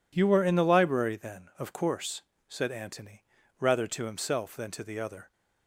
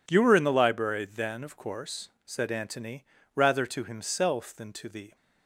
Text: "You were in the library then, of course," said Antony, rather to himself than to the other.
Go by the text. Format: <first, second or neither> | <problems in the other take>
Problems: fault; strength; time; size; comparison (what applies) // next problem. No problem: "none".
first | stops before "other"; at 5.1 s